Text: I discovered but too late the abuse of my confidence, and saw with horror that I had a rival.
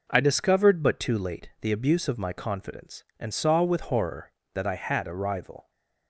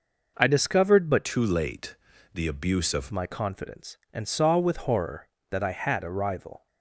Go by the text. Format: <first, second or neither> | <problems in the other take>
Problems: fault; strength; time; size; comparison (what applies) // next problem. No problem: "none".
first | changes voice from "too" to "of"; from 1.2 to 3.1 s; 1.9 s long // pauses between "late" and "the"; at 1.9 s; 0.38 s long